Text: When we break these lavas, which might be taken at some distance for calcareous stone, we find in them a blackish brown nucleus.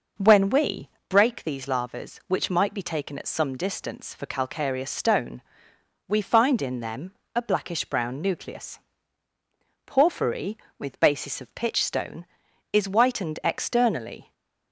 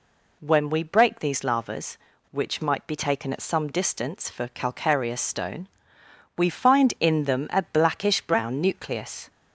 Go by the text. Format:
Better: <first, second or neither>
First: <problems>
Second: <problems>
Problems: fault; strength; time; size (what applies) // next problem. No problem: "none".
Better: second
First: pauses between "we" and "break"; slight; at 0.9 s; 0.18 s long // pauses between "them" and "a"; slight; at 7.1 s; 0.22 s long // goes on to say "Porphyry with basis of pitch stone is whitened externally"; strong; from 9.8 s on; 4.4 s long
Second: none